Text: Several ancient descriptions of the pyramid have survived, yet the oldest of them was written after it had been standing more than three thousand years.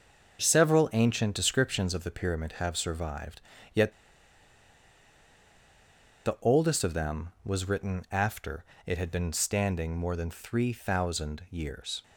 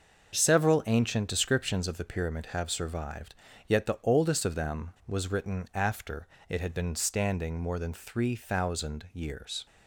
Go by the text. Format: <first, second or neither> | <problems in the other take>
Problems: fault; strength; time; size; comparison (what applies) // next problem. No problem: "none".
second | starts louder than the rest; until 1.4 s; 6.5 dB; also in the second // pauses between "yet" and "the"; strong; at 3.9 s; 2.3 s long // pauses between "after" and "it"; slight; at 8.6 s; 0.22 s long; slight in the second